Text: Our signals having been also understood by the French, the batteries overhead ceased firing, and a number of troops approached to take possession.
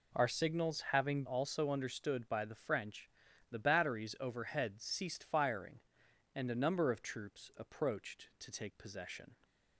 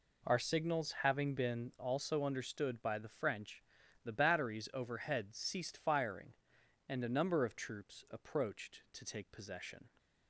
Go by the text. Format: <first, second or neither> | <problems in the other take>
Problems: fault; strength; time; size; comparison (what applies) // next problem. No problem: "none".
second | skips "been"; at 1.2 s